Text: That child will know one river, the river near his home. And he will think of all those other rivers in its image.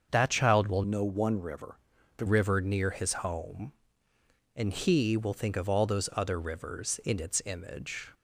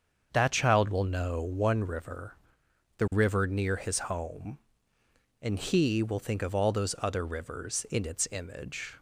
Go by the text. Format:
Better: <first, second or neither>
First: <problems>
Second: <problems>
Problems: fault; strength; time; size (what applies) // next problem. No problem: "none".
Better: second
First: starts louder than the rest; until 1.1 s; 6.5 dB // changes voice from "know" to "the"; from 0.8 to 2.2 s; 1.4 s long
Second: starts louder than the rest; until 1.3 s; 7 dB